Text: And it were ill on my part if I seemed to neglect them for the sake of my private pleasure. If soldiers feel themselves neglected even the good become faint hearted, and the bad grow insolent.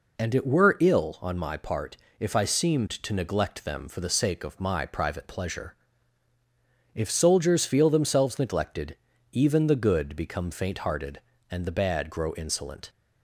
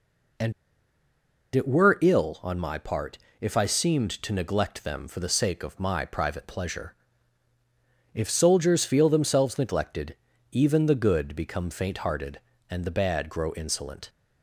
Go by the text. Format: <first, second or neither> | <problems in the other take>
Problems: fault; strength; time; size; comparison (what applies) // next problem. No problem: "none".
first | pauses between "And" and "it"; at 0.5 s; 1.0 s long // pauses between "part" and "if"; slight; at 3.1 s; 0.24 s long; slight in the first // pauses between "neglected" and "even"; slight; at 10.1 s; 0.36 s long; slight in the first